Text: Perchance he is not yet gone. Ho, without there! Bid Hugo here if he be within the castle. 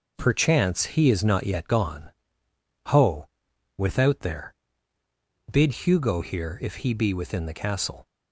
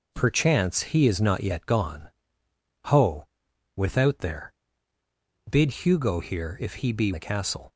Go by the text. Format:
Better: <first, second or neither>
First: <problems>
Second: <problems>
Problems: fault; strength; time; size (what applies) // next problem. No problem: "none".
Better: first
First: none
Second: skips "within"; at 7.1 s